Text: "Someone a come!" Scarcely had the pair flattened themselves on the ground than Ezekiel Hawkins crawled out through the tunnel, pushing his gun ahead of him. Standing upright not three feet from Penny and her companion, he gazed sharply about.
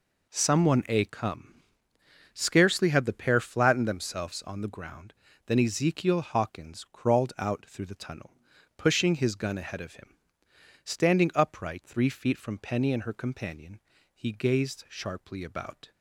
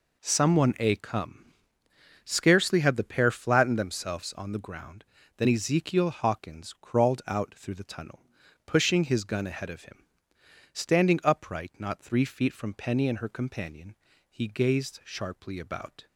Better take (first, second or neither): second